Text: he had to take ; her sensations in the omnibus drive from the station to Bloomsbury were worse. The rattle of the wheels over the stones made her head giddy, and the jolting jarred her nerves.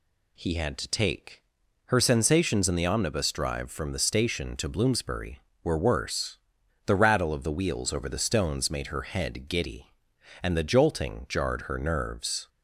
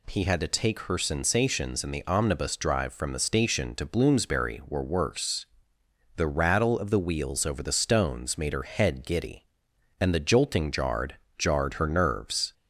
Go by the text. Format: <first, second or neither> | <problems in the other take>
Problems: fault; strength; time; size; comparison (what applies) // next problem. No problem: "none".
first | says "jarred" twice; at 11.3 s